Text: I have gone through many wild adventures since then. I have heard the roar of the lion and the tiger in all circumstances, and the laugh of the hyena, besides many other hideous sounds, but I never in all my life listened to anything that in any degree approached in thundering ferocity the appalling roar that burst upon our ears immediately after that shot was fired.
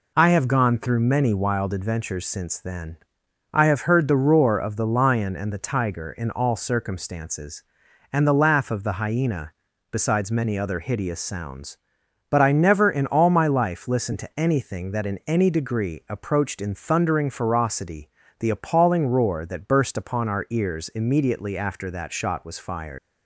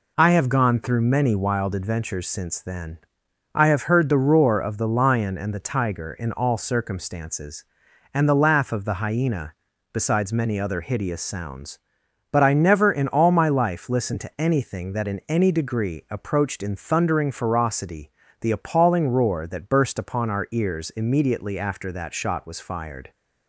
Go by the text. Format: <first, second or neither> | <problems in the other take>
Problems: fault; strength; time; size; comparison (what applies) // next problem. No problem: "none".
second | pauses between "ferocity" and "the"; slight; at 18.1 s; 0.26 s long; slight in the second // leaves "fired" unfinished; at 22.9 s; 105 ms